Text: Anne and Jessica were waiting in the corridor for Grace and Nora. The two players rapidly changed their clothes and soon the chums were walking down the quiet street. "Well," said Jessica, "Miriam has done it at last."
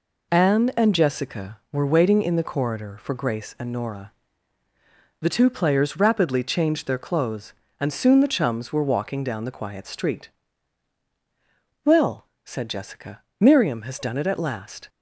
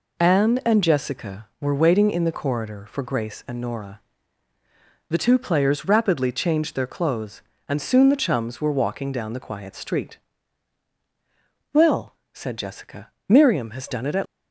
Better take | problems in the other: first | stops before "last"; at 14.2 s

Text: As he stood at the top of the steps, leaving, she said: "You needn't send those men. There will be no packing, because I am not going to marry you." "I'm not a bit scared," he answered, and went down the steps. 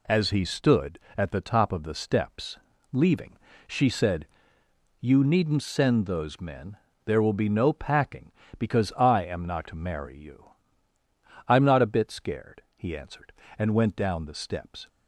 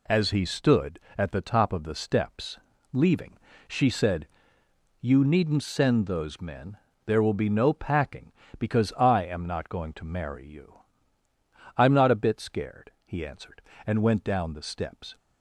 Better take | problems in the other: second | skips "going"; at 9.6 s

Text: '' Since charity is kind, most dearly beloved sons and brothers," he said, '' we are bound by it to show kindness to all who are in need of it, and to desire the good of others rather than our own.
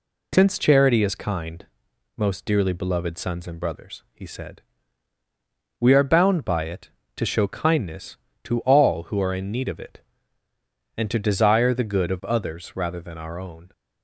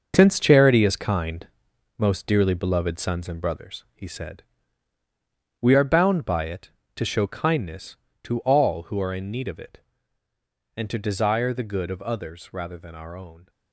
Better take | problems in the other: first | gets quieter; throughout; 6.5 dB

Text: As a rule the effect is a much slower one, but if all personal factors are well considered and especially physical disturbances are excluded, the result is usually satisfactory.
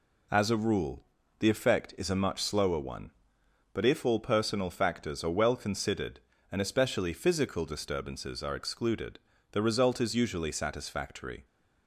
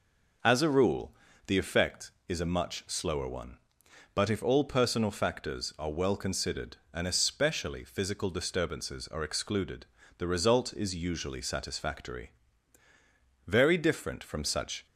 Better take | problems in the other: first | pauses between "rule" and "the"; slight; at 1.1 s; 0.36 s long; slight in the first // goes on to say "Very different from such"; from 13.4 s on; 1.3 s long

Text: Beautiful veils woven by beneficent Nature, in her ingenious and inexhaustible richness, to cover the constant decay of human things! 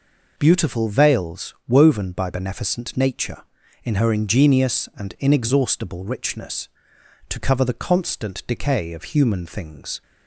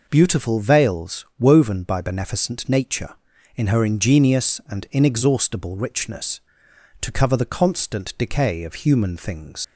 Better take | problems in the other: first | leaves "things" unfinished; at 9.6 s; 75 ms

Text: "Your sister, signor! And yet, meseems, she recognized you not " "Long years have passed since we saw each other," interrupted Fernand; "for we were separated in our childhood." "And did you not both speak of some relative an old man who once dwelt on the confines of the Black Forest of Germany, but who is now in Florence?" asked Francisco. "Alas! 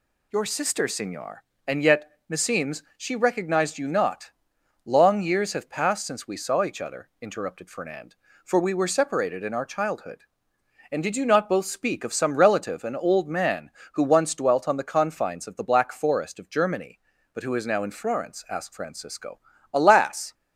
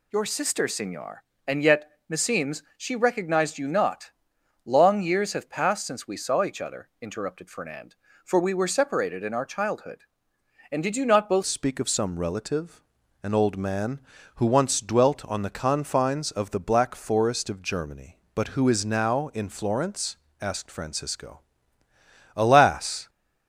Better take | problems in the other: first | changes voice at "speak"; from 11.4 s on; 11.6 s long // pauses between "relative" and "an"; at 12.8 s; 0.40 s long

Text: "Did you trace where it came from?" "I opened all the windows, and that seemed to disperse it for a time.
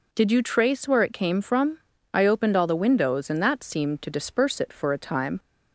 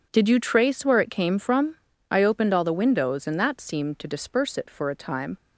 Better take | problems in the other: first | gets quieter; strong; throughout; 11.5 dB

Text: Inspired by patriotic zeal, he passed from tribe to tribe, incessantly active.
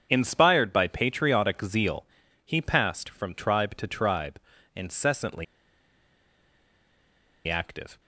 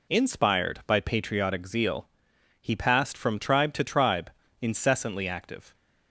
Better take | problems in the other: second | starts louder than the rest; strong; until 1.1 s; 7.5 dB // pauses between "incessantly" and "active"; strong; at 5.4 s; 2.0 s long

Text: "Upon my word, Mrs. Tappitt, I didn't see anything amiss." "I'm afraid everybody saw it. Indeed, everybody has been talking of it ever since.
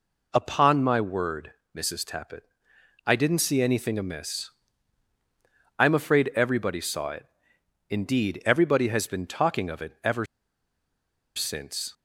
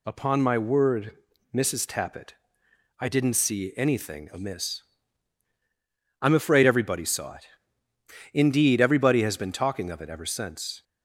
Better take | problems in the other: second | pauses between "ever" and "since"; at 10.2 s; 1.1 s long

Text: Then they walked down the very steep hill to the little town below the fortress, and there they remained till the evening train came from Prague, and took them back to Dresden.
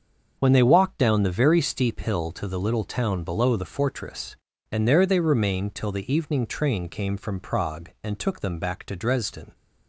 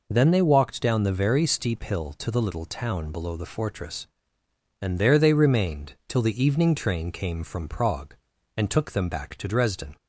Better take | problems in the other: second | starts louder than the rest; until 1.3 s; 6.5 dB // says "When" for "Then"; at 0.3 s

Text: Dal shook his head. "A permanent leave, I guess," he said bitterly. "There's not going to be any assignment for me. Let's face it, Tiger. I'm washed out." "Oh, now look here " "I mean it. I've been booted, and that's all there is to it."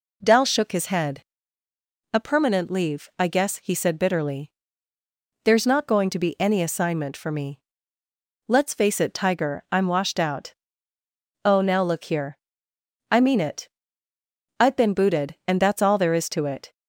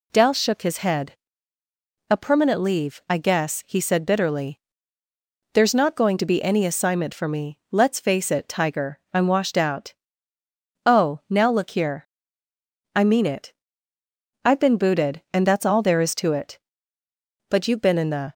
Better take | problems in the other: first | goes on to say "But you've been in the"; noticeable; from 17.5 s on; 0.82 s long

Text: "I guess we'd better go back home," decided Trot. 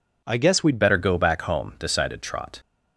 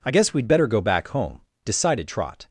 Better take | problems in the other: second | changes voice at "better"; from 0.7 s on; 1.8 s long

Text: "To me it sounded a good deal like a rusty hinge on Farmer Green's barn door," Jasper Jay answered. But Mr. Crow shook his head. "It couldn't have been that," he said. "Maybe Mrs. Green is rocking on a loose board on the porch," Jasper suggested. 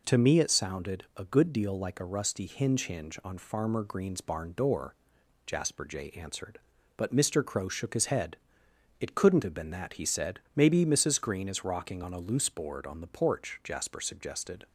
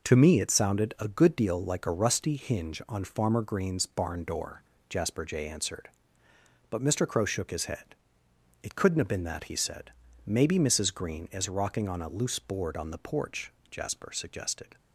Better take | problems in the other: second | says "hinge" twice; at 2.8 s

